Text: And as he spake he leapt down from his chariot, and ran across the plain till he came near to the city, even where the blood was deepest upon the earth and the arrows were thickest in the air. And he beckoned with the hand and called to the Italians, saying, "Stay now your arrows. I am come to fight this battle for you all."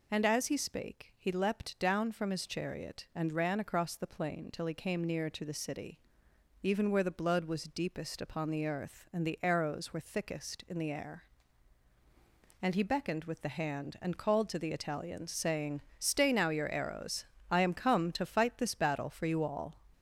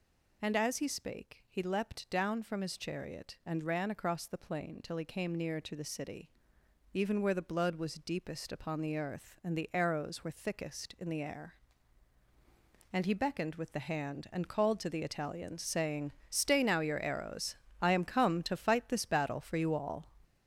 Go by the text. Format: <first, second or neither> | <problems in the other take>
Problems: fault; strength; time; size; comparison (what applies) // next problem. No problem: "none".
first | gets louder; throughout; 6.5 dB